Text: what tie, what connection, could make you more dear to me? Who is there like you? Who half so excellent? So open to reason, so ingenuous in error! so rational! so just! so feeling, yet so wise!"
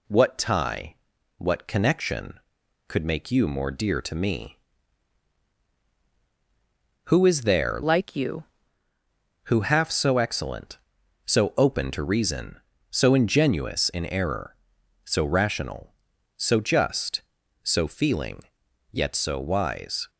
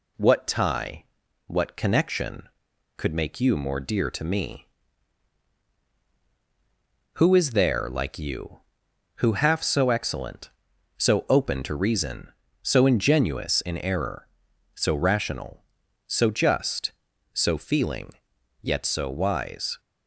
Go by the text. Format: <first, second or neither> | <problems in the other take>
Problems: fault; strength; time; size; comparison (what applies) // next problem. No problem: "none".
second | changes voice from "like" to "you"; from 7.8 to 8.4 s; 0.6 s long